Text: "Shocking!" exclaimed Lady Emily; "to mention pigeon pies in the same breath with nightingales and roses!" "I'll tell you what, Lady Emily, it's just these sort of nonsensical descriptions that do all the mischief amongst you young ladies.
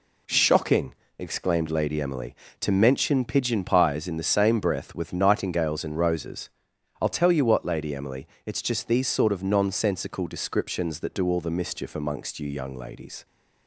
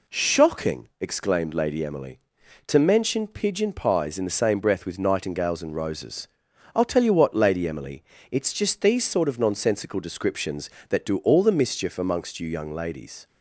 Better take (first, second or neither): neither